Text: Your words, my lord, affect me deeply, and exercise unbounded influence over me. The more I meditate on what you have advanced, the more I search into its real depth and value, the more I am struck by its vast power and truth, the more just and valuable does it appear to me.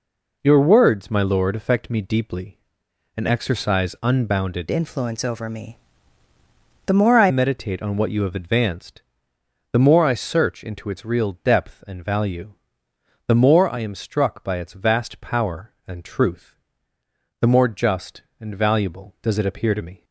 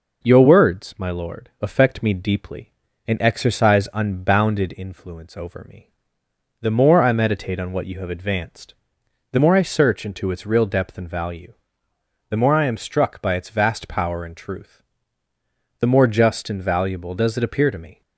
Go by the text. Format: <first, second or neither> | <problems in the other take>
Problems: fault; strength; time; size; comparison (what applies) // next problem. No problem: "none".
second | changes voice from "influence" to "I"; from 4.6 to 7.2 s; 2.6 s long